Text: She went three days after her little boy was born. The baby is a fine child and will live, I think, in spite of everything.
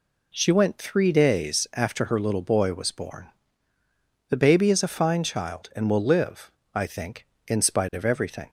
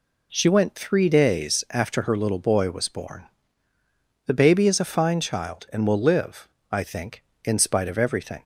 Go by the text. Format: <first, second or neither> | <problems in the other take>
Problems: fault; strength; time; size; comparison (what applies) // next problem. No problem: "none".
neither | none